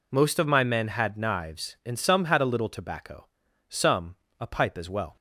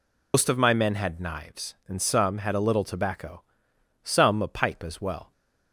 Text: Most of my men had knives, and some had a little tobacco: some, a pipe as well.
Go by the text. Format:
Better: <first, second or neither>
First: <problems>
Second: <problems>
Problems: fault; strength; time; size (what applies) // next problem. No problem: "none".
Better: first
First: none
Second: loses the start of "Most"; at 0.3 s; 125 ms